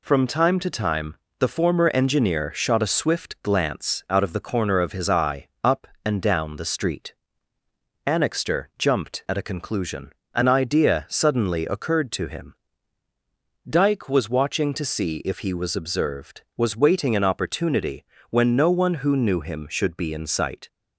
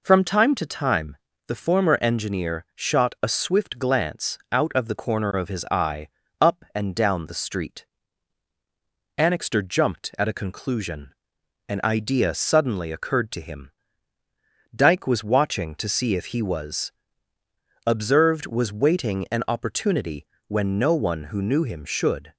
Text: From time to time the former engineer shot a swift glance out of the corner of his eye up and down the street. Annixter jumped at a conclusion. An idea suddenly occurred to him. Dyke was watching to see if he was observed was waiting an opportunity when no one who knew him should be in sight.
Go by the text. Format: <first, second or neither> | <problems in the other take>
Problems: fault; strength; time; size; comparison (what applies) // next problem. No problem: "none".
first | pauses between "time" and "the"; slight; at 1.1 s; 0.32 s long; slight in the first // pauses between "eye" and "up"; slight; at 6.0 s; 0.30 s long; slight in the first // pauses between "was" and "observed"; noticeable; at 16.9 s; 0.96 s long // pauses between "opportunity" and "when"; slight; at 20.2 s; 0.20 s long; slight in the first // stops before "be in sight"; at 22.3 s